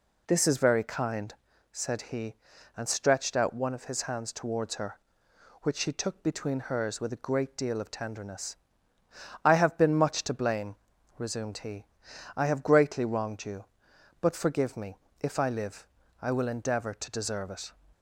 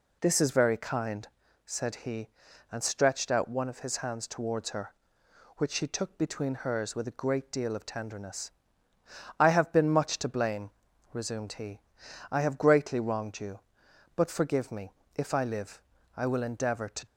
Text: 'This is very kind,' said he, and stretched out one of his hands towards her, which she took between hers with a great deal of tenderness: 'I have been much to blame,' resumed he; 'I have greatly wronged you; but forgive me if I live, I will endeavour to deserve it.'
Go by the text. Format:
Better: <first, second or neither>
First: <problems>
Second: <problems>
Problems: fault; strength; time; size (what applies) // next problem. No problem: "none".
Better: first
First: pauses between "me" and "if"; slight; at 14.9 s; 0.22 s long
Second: pauses between "me" and "if"; slight; at 14.9 s; 0.22 s long // stops before "deserve it"; at 17.0 s